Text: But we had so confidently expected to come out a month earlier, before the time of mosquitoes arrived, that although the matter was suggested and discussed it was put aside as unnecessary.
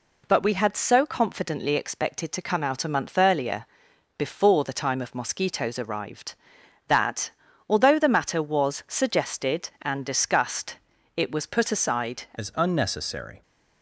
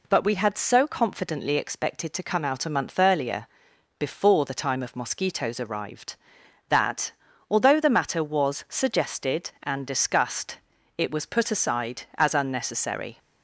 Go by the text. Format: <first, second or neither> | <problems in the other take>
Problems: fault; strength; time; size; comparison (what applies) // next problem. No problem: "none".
second | pauses between "that" and "although"; at 7.3 s; 0.38 s long; also in the second // pauses between "discussed" and "it"; at 10.7 s; 0.40 s long; also in the second // changes voice at "as"; from 12.3 s on; 1.1 s long